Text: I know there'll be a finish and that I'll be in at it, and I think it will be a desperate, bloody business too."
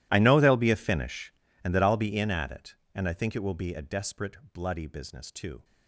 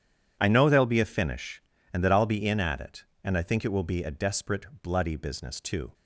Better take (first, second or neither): second